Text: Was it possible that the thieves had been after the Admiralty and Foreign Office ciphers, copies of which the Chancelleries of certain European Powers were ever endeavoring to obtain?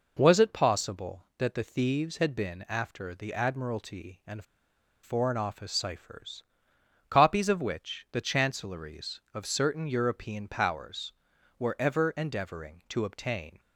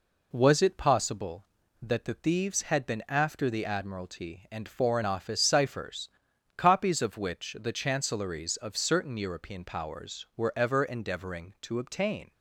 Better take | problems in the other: second | pauses between "and" and "Foreign"; noticeable; at 4.4 s; 0.59 s long

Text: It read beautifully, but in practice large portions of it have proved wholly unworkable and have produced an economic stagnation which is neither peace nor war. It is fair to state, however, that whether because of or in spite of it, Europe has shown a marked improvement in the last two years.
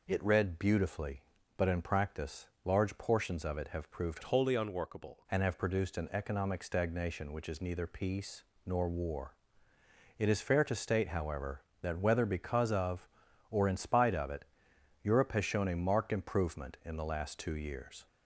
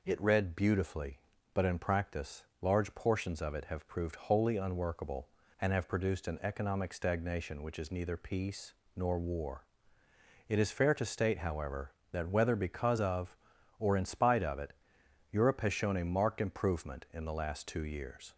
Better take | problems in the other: second | pauses between "practice" and "large"; slight; at 2.4 s; 0.18 s long; slight in the second // changes voice from "wholly" to "unworkable"; from 4.2 to 5.2 s; 1.0 s long // pauses between "peace" and "nor"; slight; at 8.4 s; 0.24 s long; slight in the second

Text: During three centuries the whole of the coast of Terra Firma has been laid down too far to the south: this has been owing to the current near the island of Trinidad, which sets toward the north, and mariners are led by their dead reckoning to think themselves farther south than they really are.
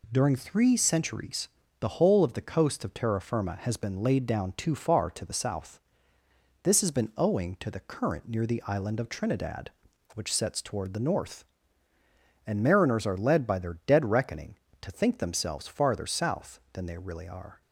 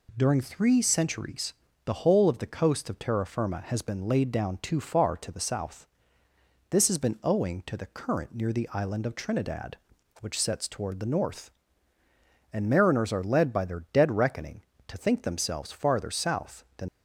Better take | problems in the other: first | pauses between "centuries" and "the"; slight; at 1.5 s; 0.32 s long; slight in the first // stops before "they really are"; at 16.8 s

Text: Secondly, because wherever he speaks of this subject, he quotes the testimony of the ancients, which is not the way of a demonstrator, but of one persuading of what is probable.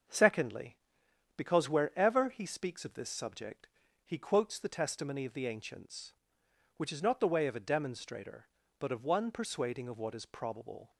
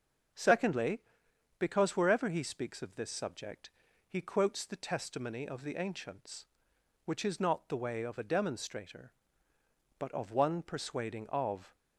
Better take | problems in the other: first | starts louder than the rest; until 1.9 s; 6.5 dB; also in the first // stops before "what is probable"; at 11.7 s

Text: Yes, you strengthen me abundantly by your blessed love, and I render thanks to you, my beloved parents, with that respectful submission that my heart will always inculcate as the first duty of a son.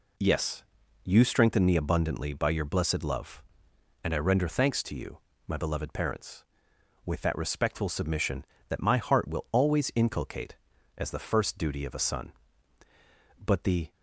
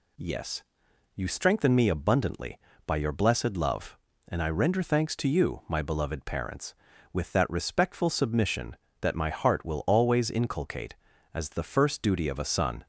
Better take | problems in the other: second | goes on to say "But the"; from 13.3 s on; 0.54 s long

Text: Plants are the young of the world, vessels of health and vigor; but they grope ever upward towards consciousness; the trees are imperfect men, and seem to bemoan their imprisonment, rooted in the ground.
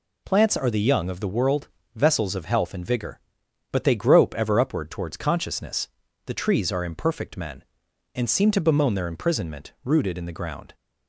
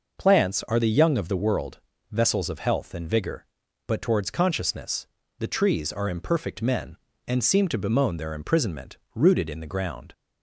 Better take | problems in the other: first | skips "they grope ever upward"; at 4.0 s

